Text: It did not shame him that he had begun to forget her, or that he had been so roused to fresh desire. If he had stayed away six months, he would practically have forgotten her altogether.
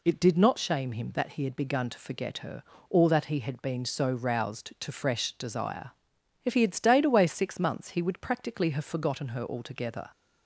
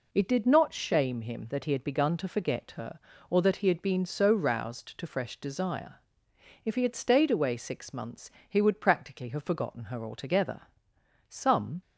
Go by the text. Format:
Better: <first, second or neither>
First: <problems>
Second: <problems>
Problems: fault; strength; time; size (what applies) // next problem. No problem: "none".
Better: first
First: none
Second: goes on to say "Some"; from 11.2 s on; 0.52 s long